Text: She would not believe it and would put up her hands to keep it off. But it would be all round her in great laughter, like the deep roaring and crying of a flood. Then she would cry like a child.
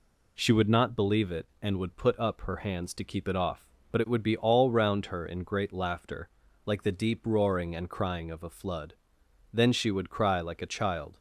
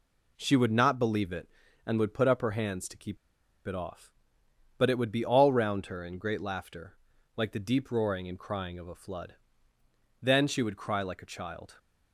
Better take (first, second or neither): first